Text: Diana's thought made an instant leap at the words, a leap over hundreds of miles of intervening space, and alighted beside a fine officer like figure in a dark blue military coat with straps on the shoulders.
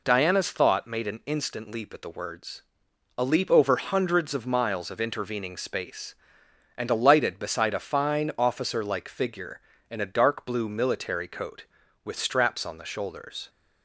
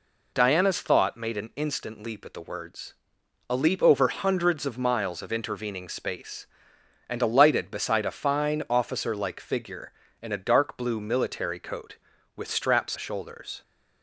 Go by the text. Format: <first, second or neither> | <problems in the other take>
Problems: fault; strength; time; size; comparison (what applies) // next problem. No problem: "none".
first | skips "on the"; at 12.9 s